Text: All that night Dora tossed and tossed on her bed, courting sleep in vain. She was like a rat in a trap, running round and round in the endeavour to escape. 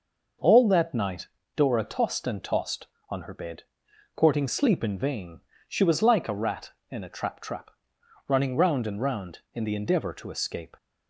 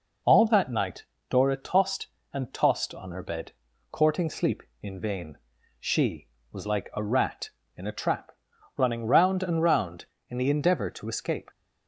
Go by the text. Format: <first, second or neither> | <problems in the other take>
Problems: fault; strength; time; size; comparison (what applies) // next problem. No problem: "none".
second | pauses between "night" and "Dora"; slight; at 1.2 s; 0.30 s long; slight in the second // says "trap" twice; at 7.4 s